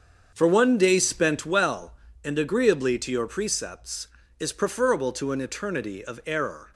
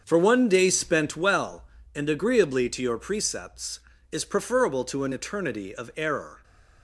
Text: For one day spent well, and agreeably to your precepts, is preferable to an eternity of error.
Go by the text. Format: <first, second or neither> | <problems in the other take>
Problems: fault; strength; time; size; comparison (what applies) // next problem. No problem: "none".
neither | starts louder than the rest; strong; the same in both